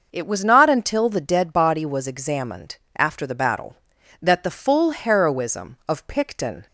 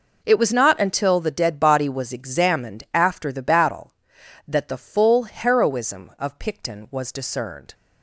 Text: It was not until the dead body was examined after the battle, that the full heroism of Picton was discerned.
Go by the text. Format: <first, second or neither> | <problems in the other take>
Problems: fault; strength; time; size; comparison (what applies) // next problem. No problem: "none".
second | pauses between "examined" and "after"; slight; at 2.7 s; 0.20 s long // stops before "was discerned"; at 6.6 s